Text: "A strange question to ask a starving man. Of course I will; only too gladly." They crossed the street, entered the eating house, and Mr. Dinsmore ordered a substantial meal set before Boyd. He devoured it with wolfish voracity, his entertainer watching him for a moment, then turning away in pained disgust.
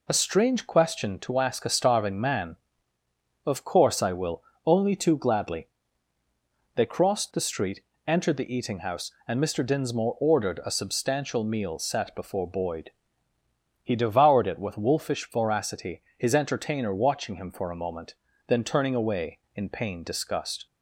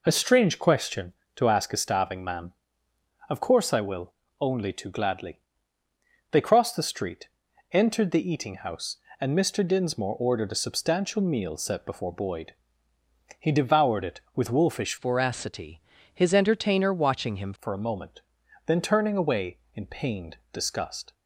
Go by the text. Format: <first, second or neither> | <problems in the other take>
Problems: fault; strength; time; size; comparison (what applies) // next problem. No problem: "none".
first | changes voice from "voracity" to "him"; from 14.9 to 17.5 s; 2.6 s long // pauses between "pained" and "disgust"; slight; at 20.3 s; 0.16 s long